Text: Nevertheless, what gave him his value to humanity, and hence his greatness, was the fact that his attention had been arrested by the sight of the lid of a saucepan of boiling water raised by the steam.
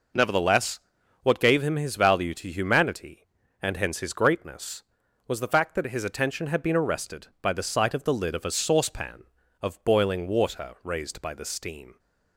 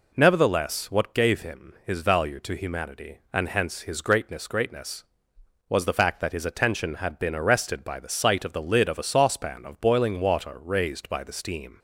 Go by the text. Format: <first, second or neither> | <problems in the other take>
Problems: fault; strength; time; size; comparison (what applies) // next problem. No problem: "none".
first | says "greatness" twice; at 4.4 s